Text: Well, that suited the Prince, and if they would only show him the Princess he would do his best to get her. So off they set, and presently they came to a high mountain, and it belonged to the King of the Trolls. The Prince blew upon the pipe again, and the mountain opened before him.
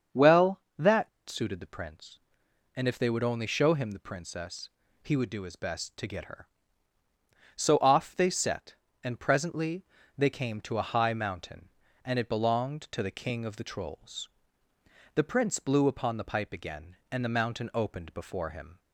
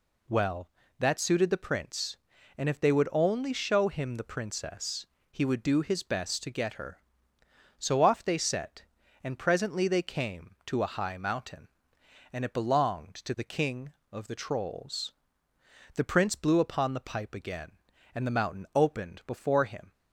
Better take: second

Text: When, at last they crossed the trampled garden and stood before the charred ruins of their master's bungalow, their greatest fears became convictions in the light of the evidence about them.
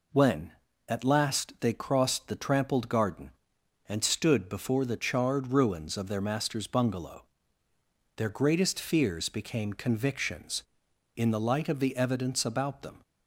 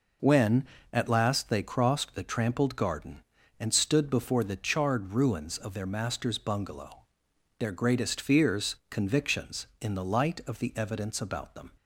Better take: first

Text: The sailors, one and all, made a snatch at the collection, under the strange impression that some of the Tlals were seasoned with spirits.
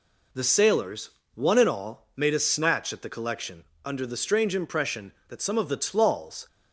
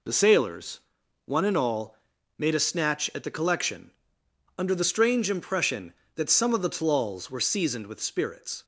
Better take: second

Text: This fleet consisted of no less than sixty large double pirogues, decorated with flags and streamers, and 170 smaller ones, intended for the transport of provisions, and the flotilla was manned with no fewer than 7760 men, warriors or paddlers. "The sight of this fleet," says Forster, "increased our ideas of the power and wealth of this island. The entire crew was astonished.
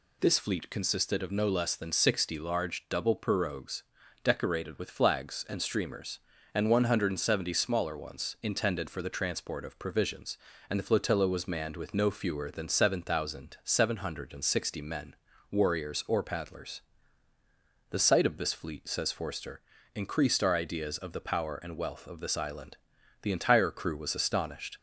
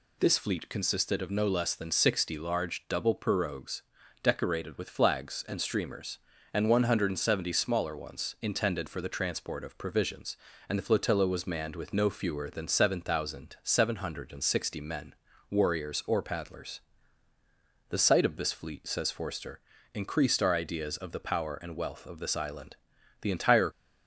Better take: first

